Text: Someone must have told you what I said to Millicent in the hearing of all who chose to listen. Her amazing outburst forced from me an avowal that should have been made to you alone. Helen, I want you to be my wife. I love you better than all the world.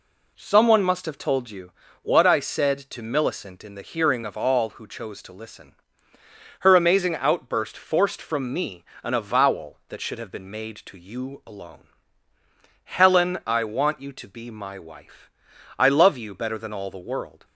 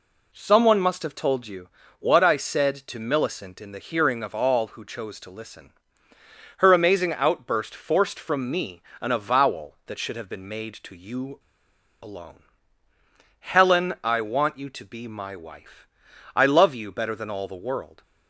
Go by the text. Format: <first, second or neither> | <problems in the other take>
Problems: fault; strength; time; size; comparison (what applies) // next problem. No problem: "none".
first | pauses between "you" and "what"; slight; at 1.6 s; 0.32 s long; slight in the first // pauses between "me" and "an"; slight; at 8.8 s; 0.20 s long; slight in the first // pauses between "you" and "alone"; noticeable; at 11.3 s; 0.62 s long